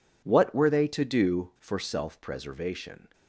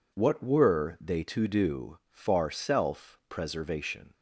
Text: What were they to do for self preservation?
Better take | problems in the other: first | says "far" for "for"; at 2.1 s

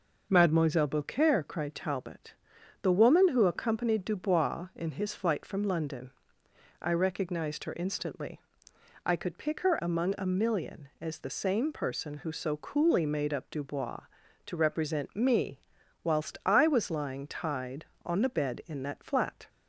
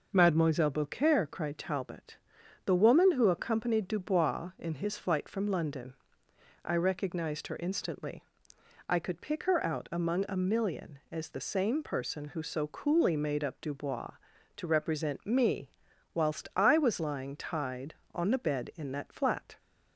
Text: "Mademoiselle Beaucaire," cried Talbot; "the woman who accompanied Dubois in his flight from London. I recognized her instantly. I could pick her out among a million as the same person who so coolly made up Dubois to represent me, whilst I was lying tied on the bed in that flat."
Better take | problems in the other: second | skips "out"; at 9.7 s

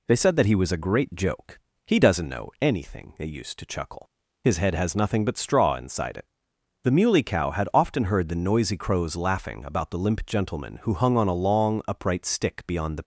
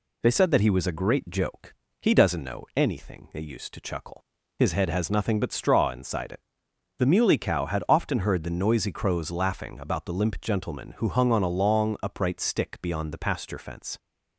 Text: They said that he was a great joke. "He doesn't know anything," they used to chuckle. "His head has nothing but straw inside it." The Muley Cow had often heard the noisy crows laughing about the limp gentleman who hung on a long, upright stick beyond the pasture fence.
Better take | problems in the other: second | stops before "pasture fence"; at 13.0 s

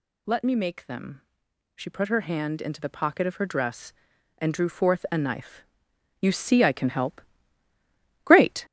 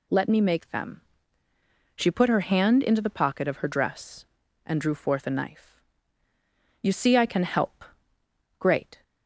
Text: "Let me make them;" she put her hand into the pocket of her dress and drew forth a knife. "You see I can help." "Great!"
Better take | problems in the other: second | gets louder; noticeable; throughout; 4.5 dB

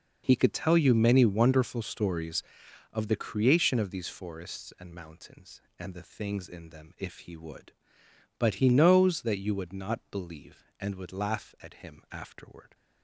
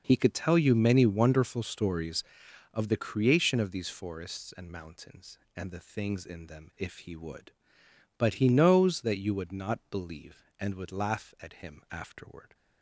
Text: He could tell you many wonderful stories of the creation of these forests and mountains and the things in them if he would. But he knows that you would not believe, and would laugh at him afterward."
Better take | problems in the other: neither | none

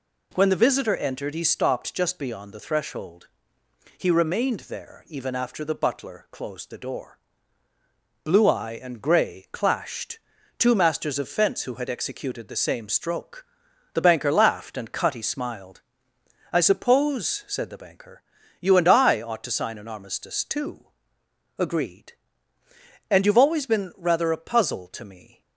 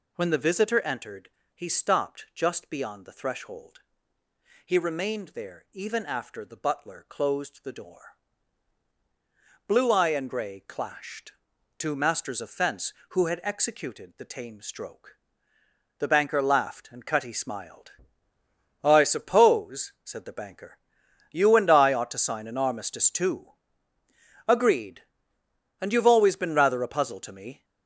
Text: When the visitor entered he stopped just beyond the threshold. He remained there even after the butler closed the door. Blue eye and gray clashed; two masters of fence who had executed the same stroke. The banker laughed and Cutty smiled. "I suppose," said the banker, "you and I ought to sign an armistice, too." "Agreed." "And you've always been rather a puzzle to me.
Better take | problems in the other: first | pauses between "entered" and "he"; slight; at 1.2 s; 0.24 s long // says "tame" for "same"; at 14.2 s

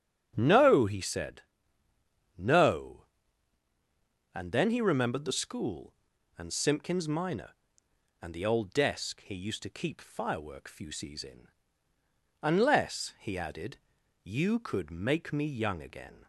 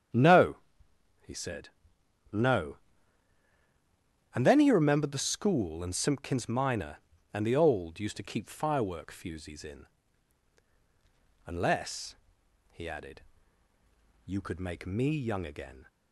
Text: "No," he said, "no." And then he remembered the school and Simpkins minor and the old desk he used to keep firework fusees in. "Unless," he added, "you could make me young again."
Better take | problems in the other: first | starts louder than the rest; strong; until 2.4 s; 8.5 dB; strong in the first // skips "desk he"; at 7.9 s

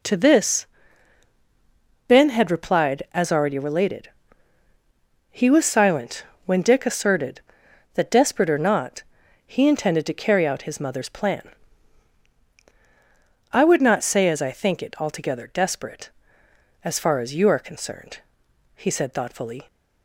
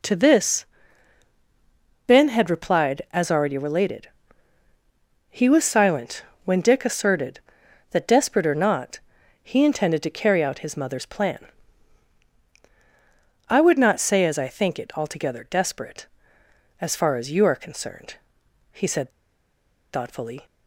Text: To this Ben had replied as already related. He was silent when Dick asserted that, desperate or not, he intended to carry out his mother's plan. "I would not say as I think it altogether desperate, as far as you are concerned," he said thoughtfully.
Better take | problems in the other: first | pauses between "this" and "Ben"; strong; at 0.6 s; 1.4 s long; strong in the first // pauses between "silent" and "when"; slight; at 6.2 s; 0.20 s long; slight in the first // pauses between "said" and "thoughtfully"; noticeable; at 19.1 s; 0.82 s long

